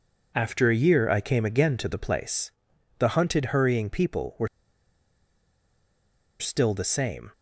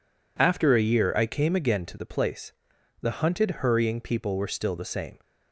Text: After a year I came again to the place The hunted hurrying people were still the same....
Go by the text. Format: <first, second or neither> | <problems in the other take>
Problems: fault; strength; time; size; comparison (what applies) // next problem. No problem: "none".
second | pauses between "place" and "The"; noticeable; at 2.5 s; 0.48 s long; noticeable in the second // pauses between "were" and "still"; strong; at 4.4 s; 1.9 s long